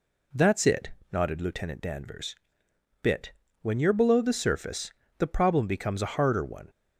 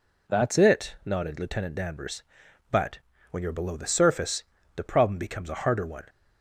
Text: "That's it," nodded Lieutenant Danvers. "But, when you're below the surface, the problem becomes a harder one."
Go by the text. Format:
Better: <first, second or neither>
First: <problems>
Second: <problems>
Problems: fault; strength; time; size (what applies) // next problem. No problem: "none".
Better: second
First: says "Bit" for "But"; at 3.0 s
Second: none